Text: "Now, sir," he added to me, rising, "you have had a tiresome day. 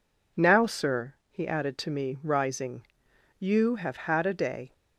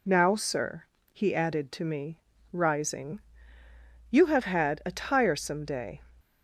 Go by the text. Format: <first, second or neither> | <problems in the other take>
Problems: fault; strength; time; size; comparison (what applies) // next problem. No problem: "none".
second | skips "tiresome"; at 4.3 s